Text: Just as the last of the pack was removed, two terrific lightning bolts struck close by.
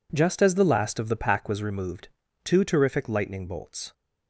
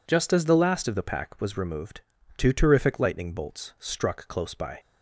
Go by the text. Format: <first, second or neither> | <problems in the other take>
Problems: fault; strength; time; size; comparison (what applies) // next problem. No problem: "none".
second | stops before "struck close by"; at 3.9 s